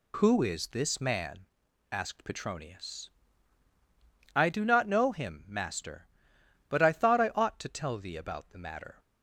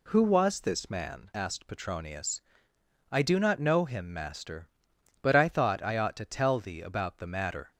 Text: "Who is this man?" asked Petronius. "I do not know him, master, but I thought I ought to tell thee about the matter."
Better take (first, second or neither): first